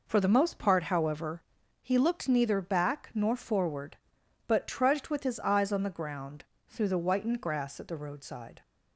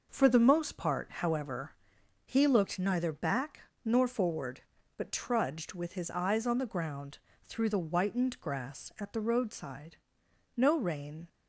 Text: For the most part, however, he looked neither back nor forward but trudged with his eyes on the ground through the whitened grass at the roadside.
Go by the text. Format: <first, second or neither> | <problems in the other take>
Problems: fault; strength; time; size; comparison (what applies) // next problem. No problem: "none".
first | pauses between "back" and "nor"; slight; at 3.5 s; 0.24 s long // pauses between "ground" and "through"; slight; at 7.1 s; 0.26 s long; slight in the first // goes on to say "No rain"; noticeable; from 10.5 s on; 0.72 s long